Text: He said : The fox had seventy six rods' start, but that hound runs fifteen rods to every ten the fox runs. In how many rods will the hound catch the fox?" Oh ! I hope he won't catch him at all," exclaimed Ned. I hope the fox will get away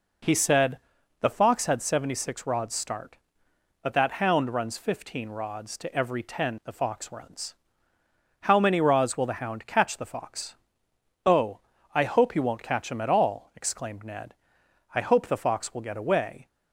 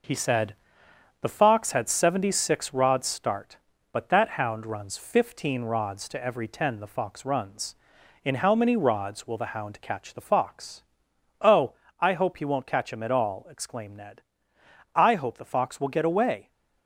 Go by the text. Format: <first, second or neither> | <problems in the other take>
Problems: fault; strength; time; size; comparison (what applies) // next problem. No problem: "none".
second | skips "In"; at 7.9 s